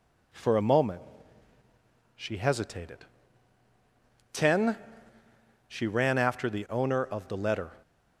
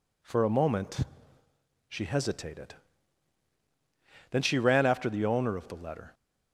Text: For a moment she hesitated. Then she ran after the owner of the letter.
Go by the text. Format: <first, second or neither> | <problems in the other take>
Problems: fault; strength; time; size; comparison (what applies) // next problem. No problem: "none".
second | pauses between "moment" and "she"; at 1.0 s; 1.1 s long; noticeable in the second // says "Ten" for "Then"; at 4.3 s